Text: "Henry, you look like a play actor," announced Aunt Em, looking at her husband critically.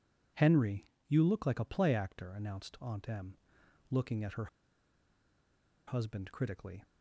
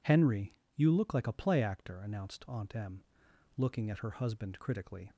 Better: second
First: pauses between "her" and "husband"; strong; at 4.4 s; 1.4 s long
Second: none

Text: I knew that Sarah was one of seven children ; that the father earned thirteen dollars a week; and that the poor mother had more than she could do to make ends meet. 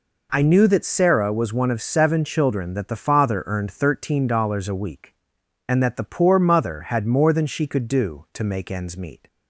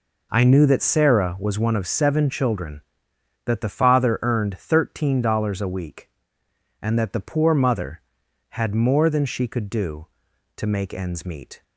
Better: neither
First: none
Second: none

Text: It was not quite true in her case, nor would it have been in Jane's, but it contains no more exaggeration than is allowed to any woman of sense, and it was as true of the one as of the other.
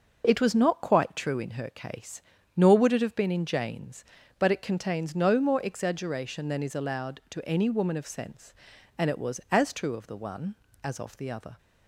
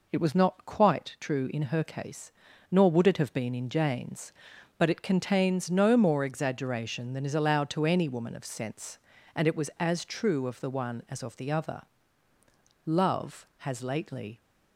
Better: first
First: none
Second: goes on to say "Love has lately"; from 12.8 s on; 1.5 s long

